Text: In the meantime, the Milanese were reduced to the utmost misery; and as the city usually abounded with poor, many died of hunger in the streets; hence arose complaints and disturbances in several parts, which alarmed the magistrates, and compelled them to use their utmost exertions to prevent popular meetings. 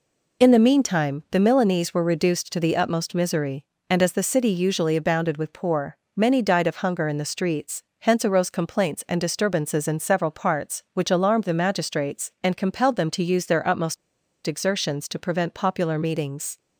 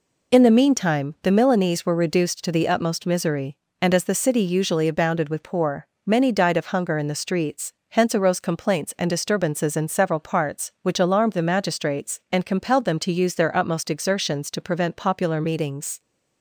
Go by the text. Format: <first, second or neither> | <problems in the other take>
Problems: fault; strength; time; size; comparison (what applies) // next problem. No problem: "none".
second | pauses between "utmost" and "exertions"; noticeable; at 13.9 s; 0.49 s long